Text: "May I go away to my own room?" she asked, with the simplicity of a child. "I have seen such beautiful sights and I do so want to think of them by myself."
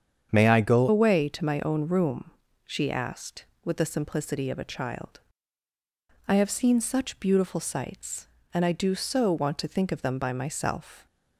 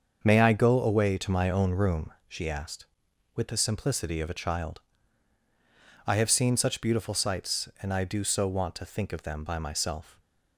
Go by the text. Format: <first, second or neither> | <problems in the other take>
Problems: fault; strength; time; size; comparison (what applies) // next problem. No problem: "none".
second | starts louder than the rest; strong; until 1.3 s; 8 dB; also in the second // changes voice at "away"; from 0.8 s on; 10.2 s long